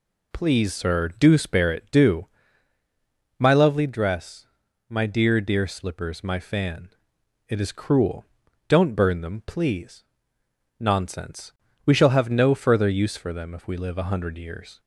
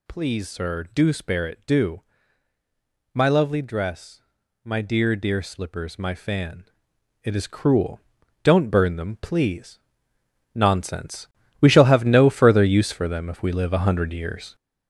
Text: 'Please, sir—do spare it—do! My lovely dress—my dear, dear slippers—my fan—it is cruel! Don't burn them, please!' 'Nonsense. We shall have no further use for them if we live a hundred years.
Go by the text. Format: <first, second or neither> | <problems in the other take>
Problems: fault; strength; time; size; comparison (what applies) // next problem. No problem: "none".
first | gets louder; throughout; 7 dB